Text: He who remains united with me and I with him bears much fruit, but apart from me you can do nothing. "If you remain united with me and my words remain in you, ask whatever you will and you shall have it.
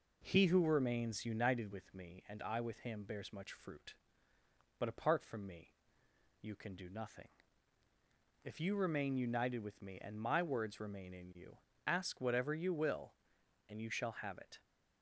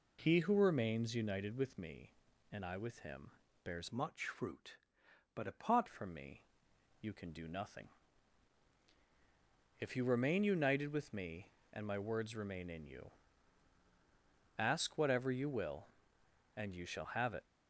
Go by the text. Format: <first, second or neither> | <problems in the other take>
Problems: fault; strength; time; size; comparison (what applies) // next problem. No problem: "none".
first | pauses between "him" and "bears"; slight; at 3.2 s; 0.34 s long // changes voice from "much" to "apart"; from 3.9 to 5.8 s; 1.9 s long // pauses between "me" and "you"; noticeable; at 6.4 s; 0.60 s long; noticeable in the first